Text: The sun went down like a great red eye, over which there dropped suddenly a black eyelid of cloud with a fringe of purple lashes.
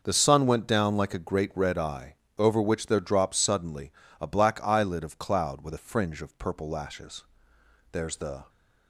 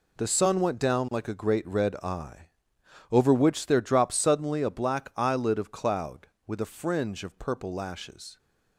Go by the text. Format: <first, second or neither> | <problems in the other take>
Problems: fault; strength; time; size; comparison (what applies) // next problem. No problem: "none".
second | starts louder than the rest; noticeable; until 1.0 s; 6 dB // pauses between "suddenly" and "a"; slight; at 3.9 s; 0.30 s long // goes on to say "There's the"; from 7.9 s on; 0.58 s long